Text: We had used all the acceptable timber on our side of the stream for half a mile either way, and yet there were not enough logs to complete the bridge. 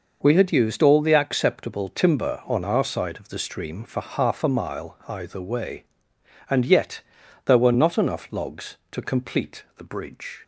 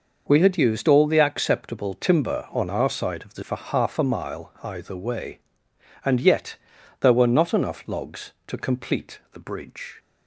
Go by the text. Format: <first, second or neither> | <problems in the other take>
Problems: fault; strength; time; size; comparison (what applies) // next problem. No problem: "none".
first | skips "stream"; at 3.4 s // pauses between "yet" and "there"; noticeable; at 6.5 s; 0.46 s long; noticeable in the first